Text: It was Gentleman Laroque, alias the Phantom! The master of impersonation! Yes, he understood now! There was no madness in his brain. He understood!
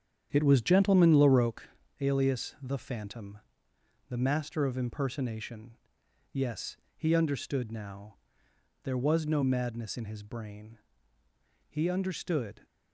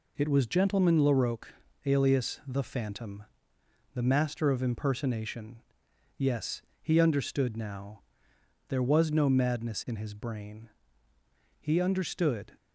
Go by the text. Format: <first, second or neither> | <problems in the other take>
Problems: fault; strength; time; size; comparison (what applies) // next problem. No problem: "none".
second | starts louder than the rest; strong; until 1.8 s; 8.5 dB